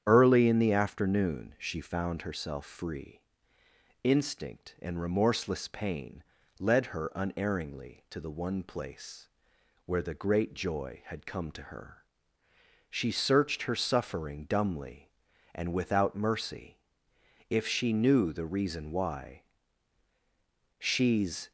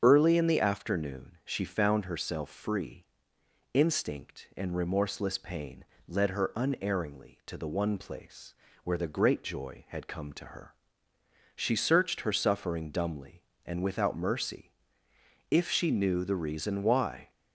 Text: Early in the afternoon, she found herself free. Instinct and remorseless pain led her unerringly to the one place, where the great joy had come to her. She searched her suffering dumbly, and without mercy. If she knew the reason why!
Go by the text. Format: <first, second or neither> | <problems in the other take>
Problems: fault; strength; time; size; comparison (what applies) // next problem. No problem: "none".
second | starts louder than the rest; strong; until 1.0 s; 9 dB; strong in the second // pauses between "pain" and "led"; slight; at 6.2 s; 0.36 s long; slight in the second // goes on to say "She's"; noticeable; from 20.7 s on; 0.72 s long